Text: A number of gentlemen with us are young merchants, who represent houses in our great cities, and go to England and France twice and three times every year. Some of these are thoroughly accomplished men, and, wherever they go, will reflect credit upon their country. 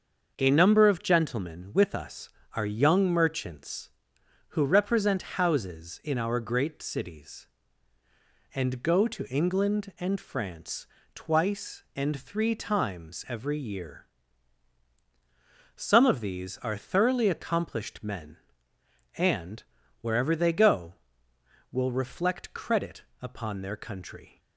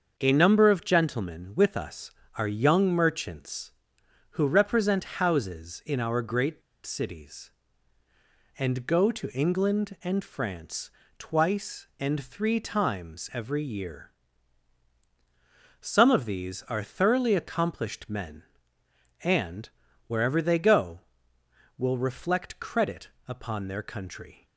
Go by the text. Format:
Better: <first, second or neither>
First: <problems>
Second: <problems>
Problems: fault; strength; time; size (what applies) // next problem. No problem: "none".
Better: first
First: starts louder than the rest; until 1.3 s; 6.5 dB // pauses between "France" and "twice"; slight; at 10.8 s; 0.28 s long // pauses between "credit" and "upon"; slight; at 23.0 s; 0.18 s long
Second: starts louder than the rest; until 1.1 s; 6.5 dB // pauses between "great" and "cities"; slight; at 6.6 s; 0.24 s long // pauses between "France" and "twice"; slight; at 10.9 s; 0.28 s long // pauses between "credit" and "upon"; slight; at 23.0 s; 0.18 s long